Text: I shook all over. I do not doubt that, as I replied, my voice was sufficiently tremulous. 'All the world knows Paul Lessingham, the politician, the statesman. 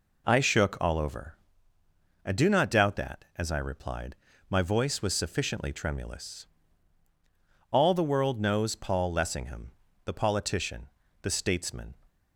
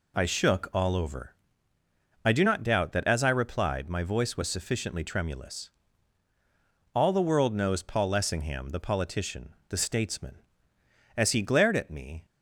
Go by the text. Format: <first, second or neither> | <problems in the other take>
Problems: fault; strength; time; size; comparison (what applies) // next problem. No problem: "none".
first | goes on to say "As he glared at me"; noticeable; from 11.1 s on; 1.0 s long